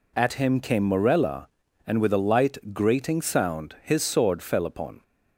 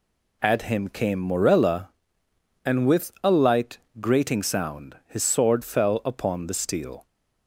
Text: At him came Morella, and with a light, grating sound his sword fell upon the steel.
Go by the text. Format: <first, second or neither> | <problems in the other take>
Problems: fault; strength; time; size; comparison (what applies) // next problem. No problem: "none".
second | stops before "the steel"; at 5.0 s